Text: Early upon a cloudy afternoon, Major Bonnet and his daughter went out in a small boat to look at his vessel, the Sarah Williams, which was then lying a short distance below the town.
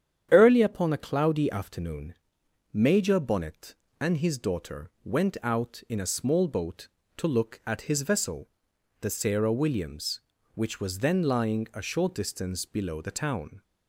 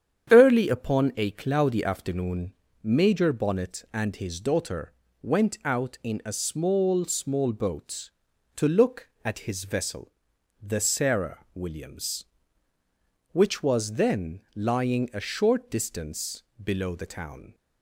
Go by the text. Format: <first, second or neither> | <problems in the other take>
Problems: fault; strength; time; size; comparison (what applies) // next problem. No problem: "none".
first | starts louder than the rest; strong; until 1.3 s; 8.5 dB; strong in the first // pauses between "daughter" and "went"; slight; at 4.9 s; 0.30 s long // says "small" twice; at 7.0 s // pauses between "distance" and "below"; slight; at 16.4 s; 0.20 s long